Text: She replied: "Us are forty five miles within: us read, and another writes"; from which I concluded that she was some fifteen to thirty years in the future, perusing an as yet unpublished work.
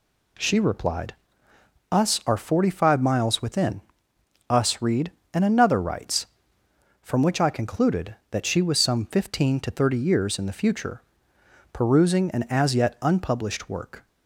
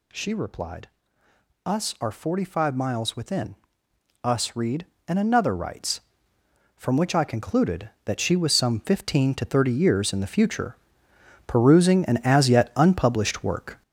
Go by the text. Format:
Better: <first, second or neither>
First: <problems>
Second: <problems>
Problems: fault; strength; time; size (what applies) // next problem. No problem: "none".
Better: first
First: none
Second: gets louder; throughout; 6.5 dB